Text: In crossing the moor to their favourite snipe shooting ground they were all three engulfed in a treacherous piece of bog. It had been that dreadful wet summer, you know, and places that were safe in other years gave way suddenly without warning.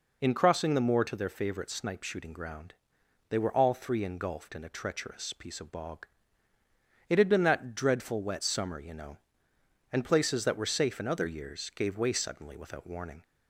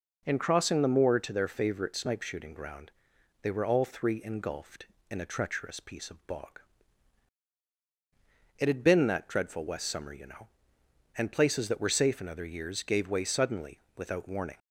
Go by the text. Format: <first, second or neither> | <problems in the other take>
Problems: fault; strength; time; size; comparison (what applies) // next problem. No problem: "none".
first | pauses between "ground" and "they"; noticeable; at 2.9 s; 0.50 s long; noticeable in the first // says "west" for "wet"; at 9.6 s // pauses between "suddenly" and "without"; slight; at 13.8 s; 0.16 s long